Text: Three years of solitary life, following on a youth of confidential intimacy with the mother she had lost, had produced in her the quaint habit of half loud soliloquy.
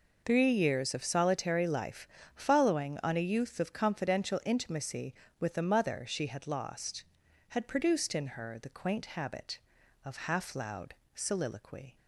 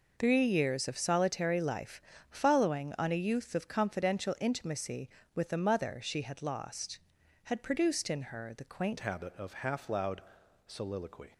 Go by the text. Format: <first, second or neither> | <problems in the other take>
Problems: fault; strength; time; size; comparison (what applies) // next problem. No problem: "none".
first | changes voice at "habit"; from 8.9 s on; 2.4 s long // pauses between "loud" and "soliloquy"; noticeable; at 10.2 s; 0.46 s long; slight in the first